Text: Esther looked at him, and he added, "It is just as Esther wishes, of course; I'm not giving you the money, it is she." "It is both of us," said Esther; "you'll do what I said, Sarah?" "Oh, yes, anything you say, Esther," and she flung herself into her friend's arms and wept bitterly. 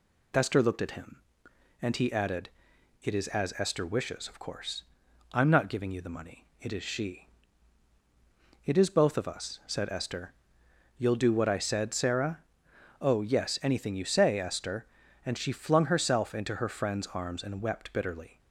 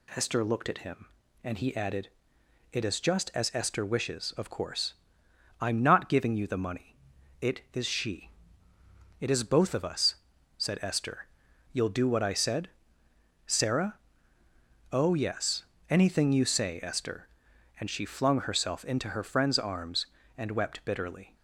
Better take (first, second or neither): second